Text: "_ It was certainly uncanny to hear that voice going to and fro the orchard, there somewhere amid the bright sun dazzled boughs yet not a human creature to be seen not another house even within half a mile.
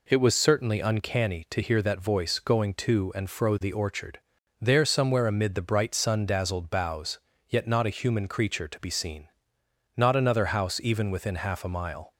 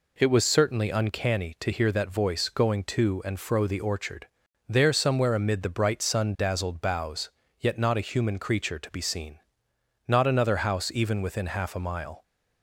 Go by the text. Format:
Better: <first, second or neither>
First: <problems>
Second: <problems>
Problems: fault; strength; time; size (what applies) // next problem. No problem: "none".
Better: neither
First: pauses between "boughs" and "yet"; slight; at 7.1 s; 0.28 s long // pauses between "seen" and "not"; noticeable; at 9.2 s; 0.68 s long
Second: pauses between "boughs" and "yet"; slight; at 7.3 s; 0.28 s long // pauses between "seen" and "not"; noticeable; at 9.3 s; 0.68 s long